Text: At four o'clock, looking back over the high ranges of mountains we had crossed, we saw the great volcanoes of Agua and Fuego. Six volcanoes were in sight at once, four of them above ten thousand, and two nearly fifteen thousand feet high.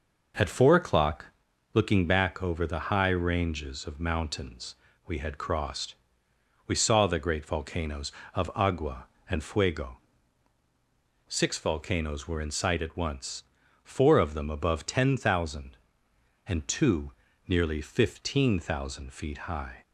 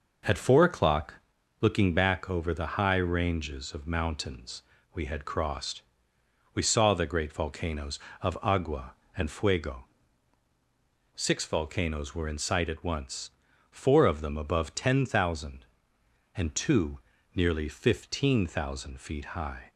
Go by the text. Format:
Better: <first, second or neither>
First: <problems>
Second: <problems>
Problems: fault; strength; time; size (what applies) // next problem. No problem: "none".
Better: neither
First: pauses between "mountains" and "we"; slight; at 4.7 s; 0.32 s long // pauses between "two" and "nearly"; slight; at 17.1 s; 0.34 s long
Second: pauses between "mountains" and "we"; slight; at 4.6 s; 0.32 s long // pauses between "two" and "nearly"; slight; at 16.9 s; 0.34 s long